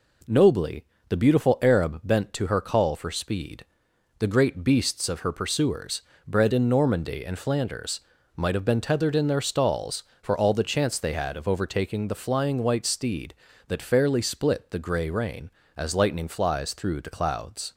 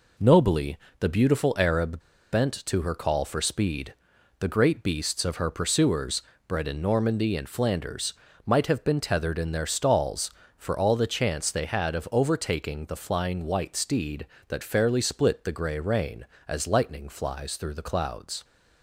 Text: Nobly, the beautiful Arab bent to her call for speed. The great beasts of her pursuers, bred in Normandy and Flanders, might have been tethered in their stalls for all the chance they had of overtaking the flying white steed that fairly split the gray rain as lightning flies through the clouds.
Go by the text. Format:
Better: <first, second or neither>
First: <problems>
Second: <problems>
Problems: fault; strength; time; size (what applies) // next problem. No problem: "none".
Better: first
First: none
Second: pauses between "Arab" and "bent"; slight; at 1.9 s; 0.33 s long